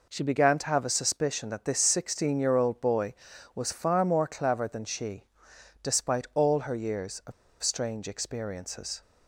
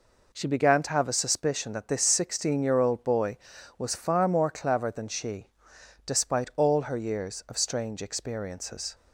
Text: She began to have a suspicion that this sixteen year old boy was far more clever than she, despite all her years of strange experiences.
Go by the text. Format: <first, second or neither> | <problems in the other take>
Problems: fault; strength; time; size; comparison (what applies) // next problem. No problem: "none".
second | pauses between "of" and "strange"; slight; at 7.3 s; 0.30 s long